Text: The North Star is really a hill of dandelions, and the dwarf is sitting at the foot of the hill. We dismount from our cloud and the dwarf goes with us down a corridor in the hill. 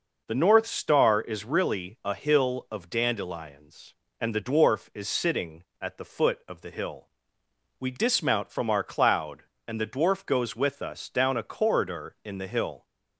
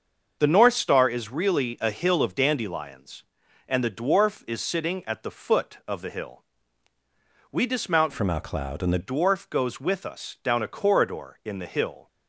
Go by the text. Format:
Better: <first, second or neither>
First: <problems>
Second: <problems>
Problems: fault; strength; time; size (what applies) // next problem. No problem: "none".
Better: first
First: none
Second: starts louder than the rest; until 1.4 s; 6.5 dB // changes voice from "from" to "the"; from 8.1 to 8.9 s; 0.8 s long